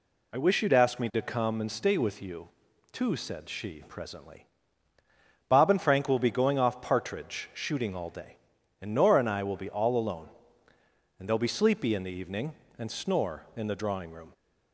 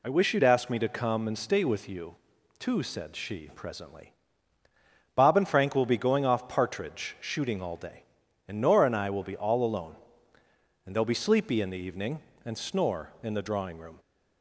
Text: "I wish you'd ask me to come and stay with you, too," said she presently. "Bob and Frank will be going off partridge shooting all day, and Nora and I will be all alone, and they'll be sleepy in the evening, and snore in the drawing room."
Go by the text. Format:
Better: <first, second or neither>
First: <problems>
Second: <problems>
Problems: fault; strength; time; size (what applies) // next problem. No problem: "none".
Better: neither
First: none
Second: none